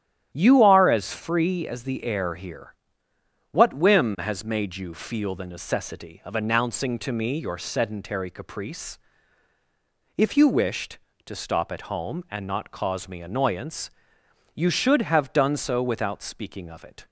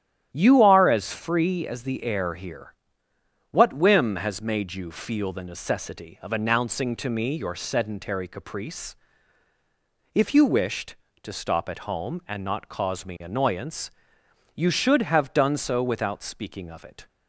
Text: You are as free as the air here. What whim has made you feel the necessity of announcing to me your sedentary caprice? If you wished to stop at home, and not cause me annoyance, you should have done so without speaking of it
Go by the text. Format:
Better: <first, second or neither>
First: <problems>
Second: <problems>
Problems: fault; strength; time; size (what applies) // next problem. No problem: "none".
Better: neither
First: starts louder than the rest; strong; until 1.3 s; 11 dB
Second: starts louder than the rest; strong; until 1.3 s; 11 dB